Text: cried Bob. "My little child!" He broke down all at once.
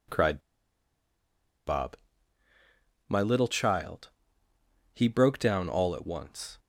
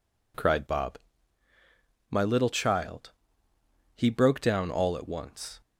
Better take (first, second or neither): second